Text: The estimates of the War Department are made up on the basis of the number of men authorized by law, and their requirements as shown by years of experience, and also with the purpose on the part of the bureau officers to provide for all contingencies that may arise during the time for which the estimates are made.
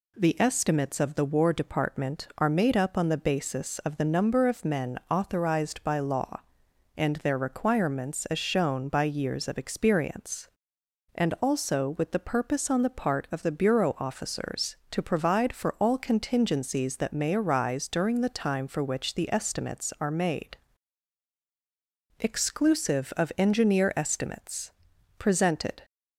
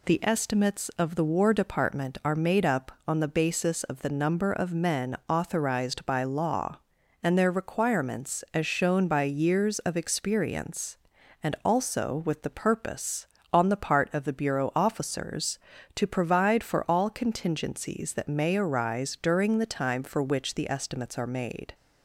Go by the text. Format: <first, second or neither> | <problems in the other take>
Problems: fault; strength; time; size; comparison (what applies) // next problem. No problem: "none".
second | goes on to say "Exclusive of engineer estimates presented"; strong; from 22.2 s on; 3.6 s long